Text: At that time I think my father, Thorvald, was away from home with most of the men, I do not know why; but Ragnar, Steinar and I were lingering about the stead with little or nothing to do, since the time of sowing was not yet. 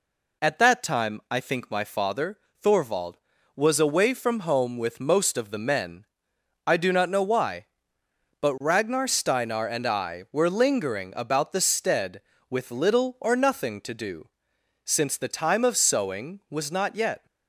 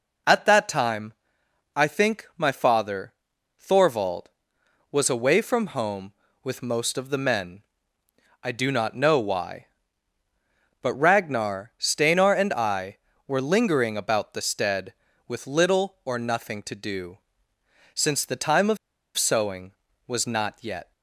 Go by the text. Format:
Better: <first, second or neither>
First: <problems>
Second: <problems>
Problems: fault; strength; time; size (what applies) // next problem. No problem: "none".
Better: first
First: none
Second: pauses between "time" and "I"; noticeable; at 1.1 s; 0.64 s long // pauses between "of" and "sowing"; at 18.7 s; 0.40 s long